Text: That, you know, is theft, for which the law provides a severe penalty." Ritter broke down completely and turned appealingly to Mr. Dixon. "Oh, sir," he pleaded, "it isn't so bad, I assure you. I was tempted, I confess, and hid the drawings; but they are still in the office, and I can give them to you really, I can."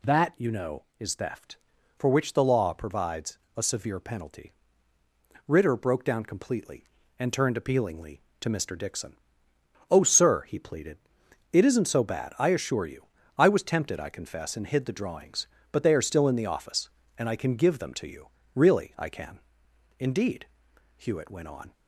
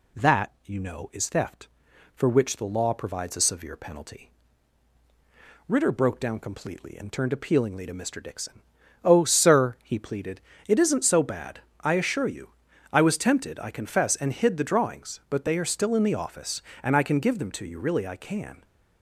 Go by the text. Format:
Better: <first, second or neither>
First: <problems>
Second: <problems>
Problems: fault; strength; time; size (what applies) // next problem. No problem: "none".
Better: second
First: pauses between "provides" and "a"; slight; at 3.3 s; 0.18 s long // pauses between "you" and "really"; slight; at 18.2 s; 0.26 s long // goes on to say "Indeed Hewitt went on"; strong; from 19.9 s on; 1.7 s long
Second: none